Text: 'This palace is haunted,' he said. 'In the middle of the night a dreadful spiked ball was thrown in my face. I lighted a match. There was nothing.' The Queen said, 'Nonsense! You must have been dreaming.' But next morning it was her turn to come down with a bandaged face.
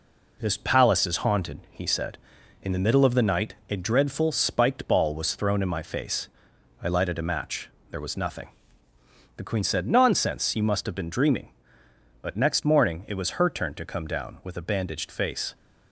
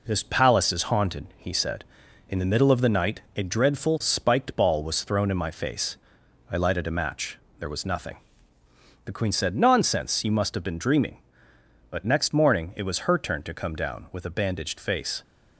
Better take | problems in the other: neither | none

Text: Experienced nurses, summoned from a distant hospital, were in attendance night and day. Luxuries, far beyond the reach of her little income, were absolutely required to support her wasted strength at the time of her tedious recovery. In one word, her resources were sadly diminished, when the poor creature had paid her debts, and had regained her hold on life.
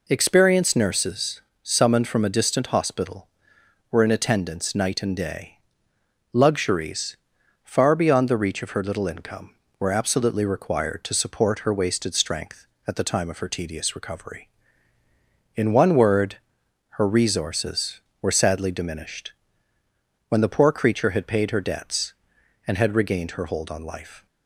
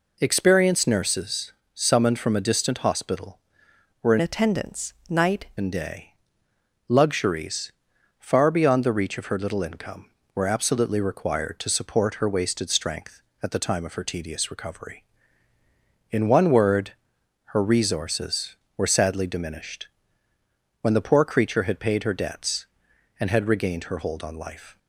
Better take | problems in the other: first | changes voice from "attendance" to "night"; from 4.2 to 5.4 s; 1.2 s long // pauses between "attendance" and "night"; slight; at 4.9 s; 0.16 s long

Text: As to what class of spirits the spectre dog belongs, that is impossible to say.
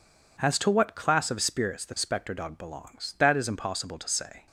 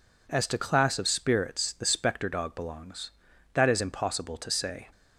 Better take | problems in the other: first | skips "what"; at 0.5 s

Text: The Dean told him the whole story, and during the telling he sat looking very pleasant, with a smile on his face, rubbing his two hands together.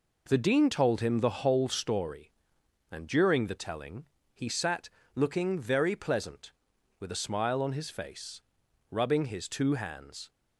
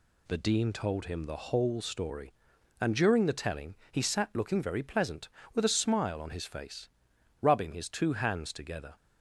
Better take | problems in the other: second | pauses between "telling" and "he"; slight; at 4.0 s; 0.28 s long; slight in the second // pauses between "sat" and "looking"; slight; at 4.8 s; 0.26 s long // stops before "together"; at 10.2 s

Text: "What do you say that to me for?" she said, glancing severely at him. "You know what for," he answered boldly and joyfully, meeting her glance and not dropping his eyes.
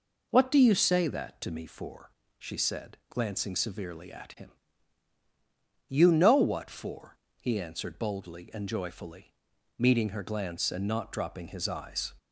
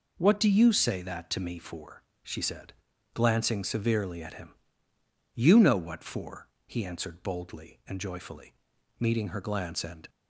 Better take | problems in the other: first | stops before "not dropping his eyes"; at 10.0 s

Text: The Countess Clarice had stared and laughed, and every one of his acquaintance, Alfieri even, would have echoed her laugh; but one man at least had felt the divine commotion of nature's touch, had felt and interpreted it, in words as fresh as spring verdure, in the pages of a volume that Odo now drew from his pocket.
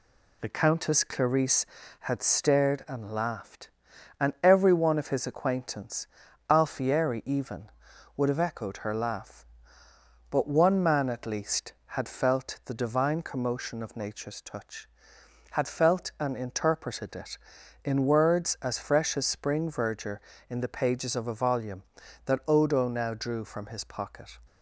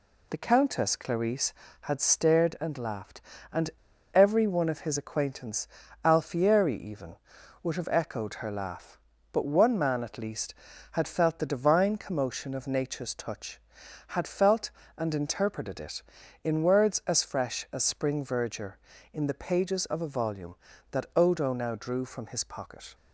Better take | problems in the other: first | pauses between "and" and "every"; at 3.7 s; 0.43 s long

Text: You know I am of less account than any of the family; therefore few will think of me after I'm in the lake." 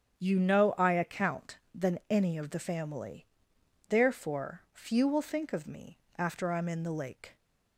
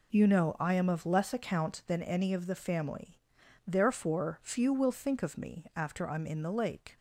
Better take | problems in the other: second | starts louder than the rest; strong; until 1.2 s; 8.5 dB // skips "am of less"; at 0.9 s // pauses between "me" and "after"; slight; at 5.9 s; 0.20 s long

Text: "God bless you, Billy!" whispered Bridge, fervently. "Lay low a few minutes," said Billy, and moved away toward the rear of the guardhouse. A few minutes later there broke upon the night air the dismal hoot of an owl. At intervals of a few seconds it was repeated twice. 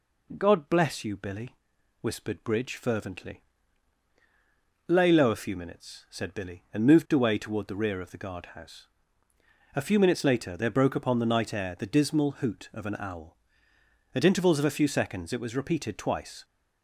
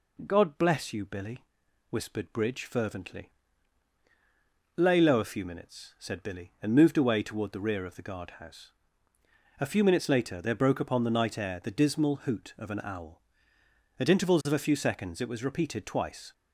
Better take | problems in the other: neither | none

